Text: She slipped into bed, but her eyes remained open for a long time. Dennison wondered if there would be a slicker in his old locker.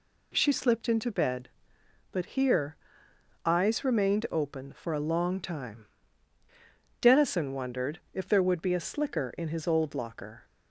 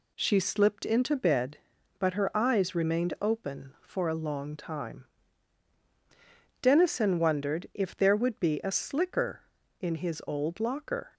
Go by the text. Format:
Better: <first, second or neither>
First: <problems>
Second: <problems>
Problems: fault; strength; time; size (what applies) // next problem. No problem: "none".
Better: second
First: says "here" for "her"; at 2.2 s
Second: none